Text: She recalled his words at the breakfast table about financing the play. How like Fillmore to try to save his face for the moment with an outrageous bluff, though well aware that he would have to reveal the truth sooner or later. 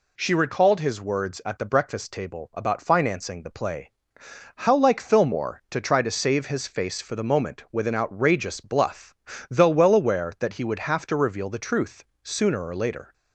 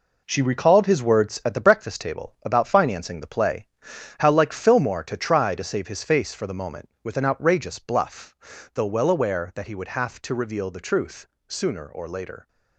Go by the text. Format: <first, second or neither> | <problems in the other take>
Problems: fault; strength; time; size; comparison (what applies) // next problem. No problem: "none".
first | gets quieter; strong; throughout; 8 dB // pauses between "truth" and "sooner"; slight; at 11.2 s; 0.24 s long; slight in the first